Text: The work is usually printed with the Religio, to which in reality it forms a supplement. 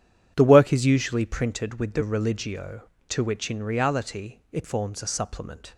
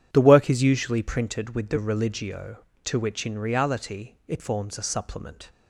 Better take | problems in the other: neither | starts louder than the rest; strong; the same in both

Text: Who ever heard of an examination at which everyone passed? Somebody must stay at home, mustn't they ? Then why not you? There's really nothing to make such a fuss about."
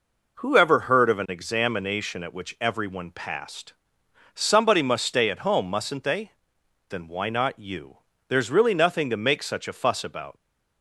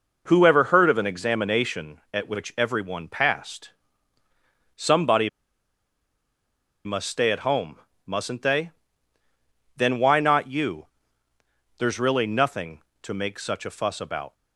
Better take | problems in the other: first | pauses between "Somebody" and "must"; strong; at 5.2 s; 1.5 s long

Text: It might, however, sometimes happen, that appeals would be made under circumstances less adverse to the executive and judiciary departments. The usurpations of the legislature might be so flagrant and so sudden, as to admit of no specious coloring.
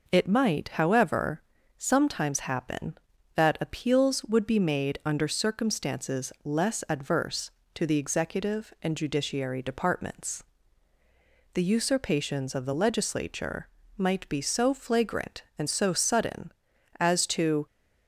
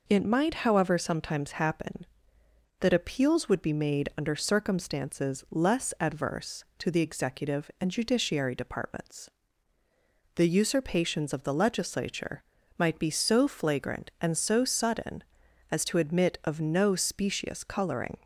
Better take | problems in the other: second | pauses between "legislature" and "might"; slight; at 13.6 s; 0.30 s long; slight in the second // stops before "admit of no specious coloring"; at 17.6 s

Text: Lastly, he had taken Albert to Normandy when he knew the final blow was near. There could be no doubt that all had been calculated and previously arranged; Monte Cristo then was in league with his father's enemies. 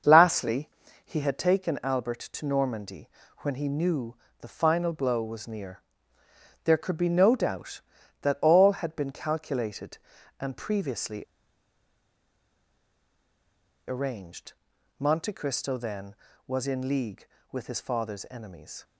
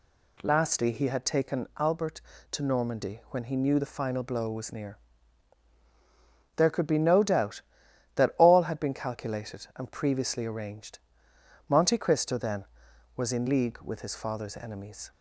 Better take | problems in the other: second | starts louder than the rest; until 1.4 s; 6.5 dB // pauses between "Normandy" and "when"; slight; at 3.0 s; 0.30 s long // pauses between "knew" and "the"; slight; at 4.1 s; 0.26 s long // pauses between "previously" and "arranged"; strong; at 11.2 s; 2.6 s long

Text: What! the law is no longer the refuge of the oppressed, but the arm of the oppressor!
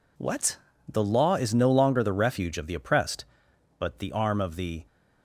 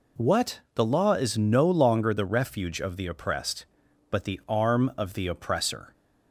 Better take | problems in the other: second | stops before "oppressor"; at 4.8 s

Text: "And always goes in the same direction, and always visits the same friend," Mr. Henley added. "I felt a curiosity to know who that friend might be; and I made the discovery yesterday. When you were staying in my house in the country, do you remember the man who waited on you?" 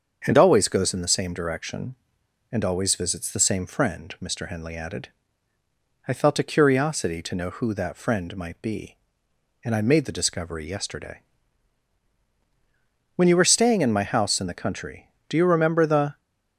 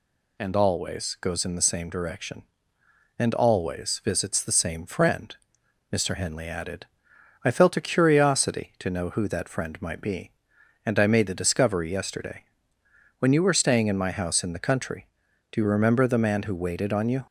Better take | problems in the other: second | starts louder than the rest; until 1.2 s; 7 dB // stops before "man who waited on you"; at 16.1 s

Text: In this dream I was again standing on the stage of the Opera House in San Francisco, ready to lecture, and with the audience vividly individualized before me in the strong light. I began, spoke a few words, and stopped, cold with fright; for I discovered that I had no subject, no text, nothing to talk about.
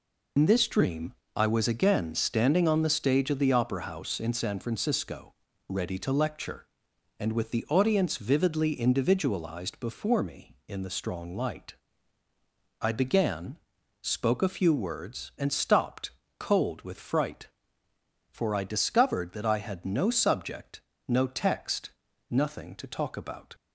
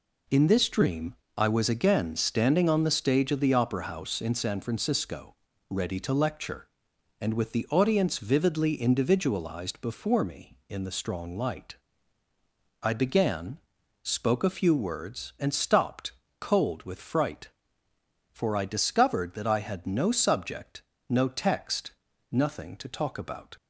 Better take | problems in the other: second | loses the start of "In"; at 0.3 s; 85 ms // pauses between "dream" and "I"; slight; at 1.1 s; 0.22 s long; slight in the second

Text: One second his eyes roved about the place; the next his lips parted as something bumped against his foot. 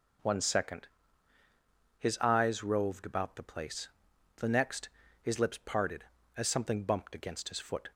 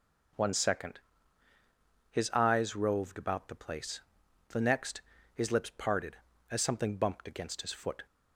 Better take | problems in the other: neither | pauses between "second" and "his"; the same in both // pauses between "next" and "his"; slight; the same in both

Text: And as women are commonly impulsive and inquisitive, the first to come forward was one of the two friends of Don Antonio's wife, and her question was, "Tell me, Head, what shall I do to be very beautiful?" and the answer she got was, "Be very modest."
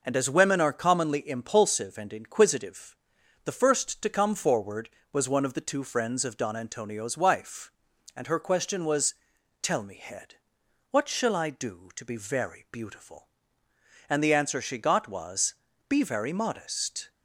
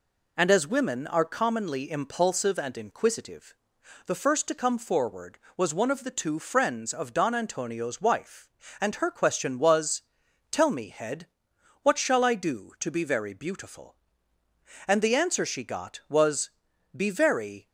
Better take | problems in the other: first | stops before "modest"; at 17.6 s

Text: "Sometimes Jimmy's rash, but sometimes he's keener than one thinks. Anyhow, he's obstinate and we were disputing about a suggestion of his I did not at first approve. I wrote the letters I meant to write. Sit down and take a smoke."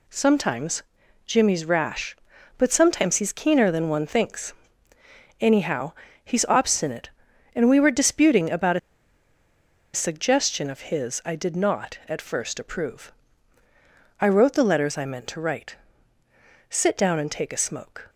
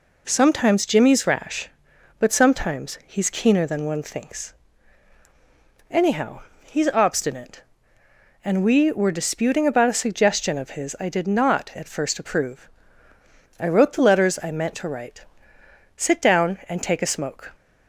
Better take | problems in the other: second | pauses between "Sometimes" and "Jimmy's"; at 0.8 s; 0.42 s long // pauses between "about" and "a"; at 8.7 s; 1.1 s long

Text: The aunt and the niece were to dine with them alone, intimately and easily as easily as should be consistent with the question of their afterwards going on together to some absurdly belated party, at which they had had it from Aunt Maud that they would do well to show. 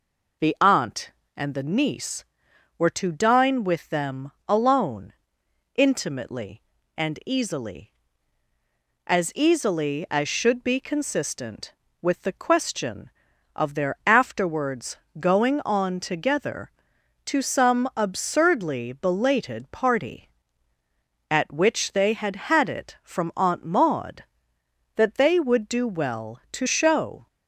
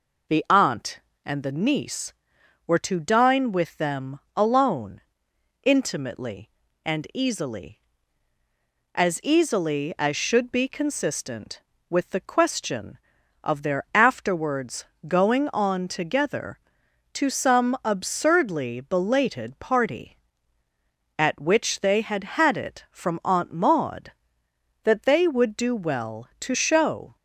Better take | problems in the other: neither | pauses between "them" and "alone"; slight; the same in both // pauses between "afterwards" and "going"; slight; the same in both

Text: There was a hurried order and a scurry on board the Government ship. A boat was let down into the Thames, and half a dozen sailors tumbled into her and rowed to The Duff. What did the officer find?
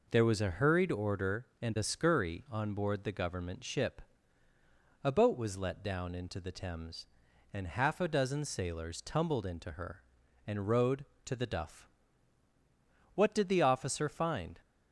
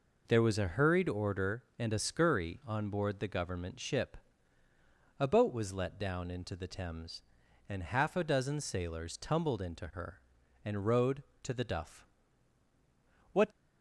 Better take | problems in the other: first | stops before "did the officer find"; at 13.5 s

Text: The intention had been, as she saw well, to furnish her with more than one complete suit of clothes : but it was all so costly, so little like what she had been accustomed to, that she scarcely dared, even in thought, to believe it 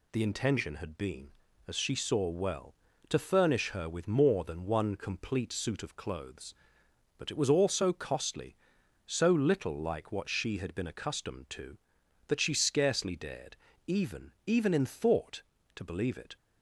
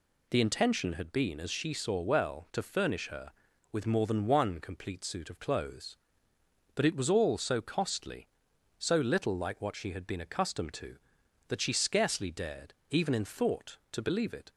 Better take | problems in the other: second | says "even" twice; at 14.4 s

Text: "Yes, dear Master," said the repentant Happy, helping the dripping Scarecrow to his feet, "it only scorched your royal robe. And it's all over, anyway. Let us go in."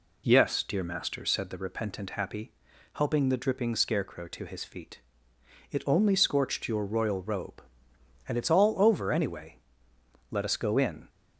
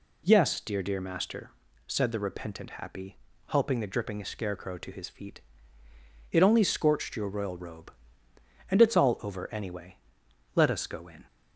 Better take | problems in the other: first | says "dear" twice; at 0.8 s

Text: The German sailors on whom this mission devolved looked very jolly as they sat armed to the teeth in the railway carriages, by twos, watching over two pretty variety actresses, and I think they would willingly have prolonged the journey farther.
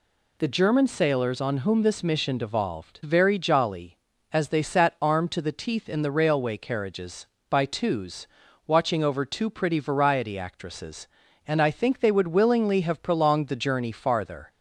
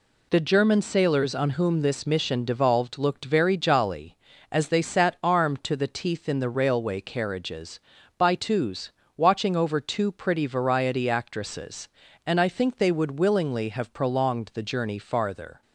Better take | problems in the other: second | skips "looked"; at 3.0 s

